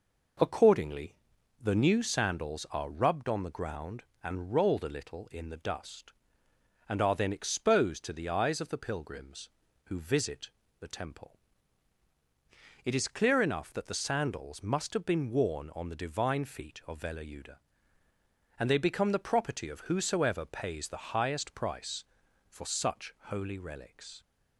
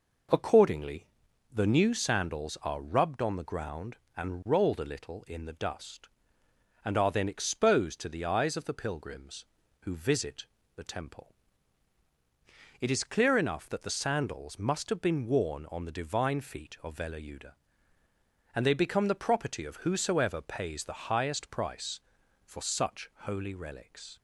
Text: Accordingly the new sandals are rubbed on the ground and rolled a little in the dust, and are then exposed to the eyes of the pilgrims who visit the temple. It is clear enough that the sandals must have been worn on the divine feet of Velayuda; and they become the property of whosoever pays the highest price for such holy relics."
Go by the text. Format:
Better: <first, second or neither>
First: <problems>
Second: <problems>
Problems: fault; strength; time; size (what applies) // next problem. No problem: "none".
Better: neither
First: pauses between "Accordingly" and "the"; noticeable; at 1.1 s; 0.46 s long // pauses between "visit" and "the"; slight; at 10.5 s; 0.28 s long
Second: pauses between "Accordingly" and "the"; noticeable; at 1.0 s; 0.46 s long // pauses between "visit" and "the"; slight; at 10.4 s; 0.28 s long